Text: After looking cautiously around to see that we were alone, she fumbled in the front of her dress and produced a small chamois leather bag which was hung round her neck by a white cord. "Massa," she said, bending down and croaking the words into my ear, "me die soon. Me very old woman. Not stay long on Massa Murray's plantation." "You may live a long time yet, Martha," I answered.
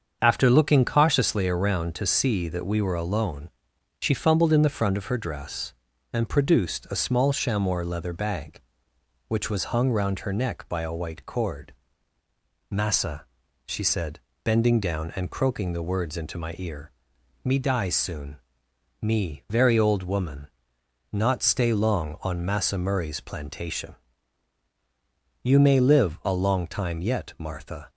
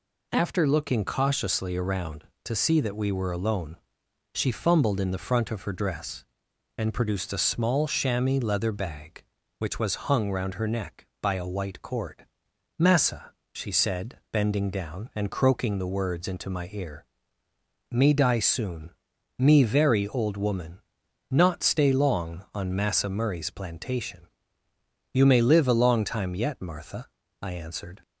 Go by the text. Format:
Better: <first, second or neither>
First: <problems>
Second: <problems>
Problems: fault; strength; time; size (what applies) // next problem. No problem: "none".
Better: second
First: starts louder than the rest; until 1.2 s; 7 dB // stops before "I answered"; at 27.8 s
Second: none